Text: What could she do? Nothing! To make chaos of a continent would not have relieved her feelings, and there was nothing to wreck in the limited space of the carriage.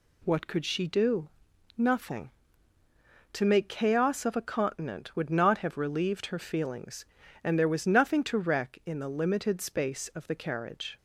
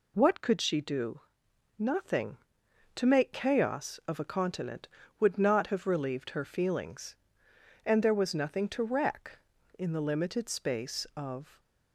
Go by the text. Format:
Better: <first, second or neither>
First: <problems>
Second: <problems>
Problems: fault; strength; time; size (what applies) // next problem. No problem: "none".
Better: first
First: none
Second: stops before "the carriage"; at 11.5 s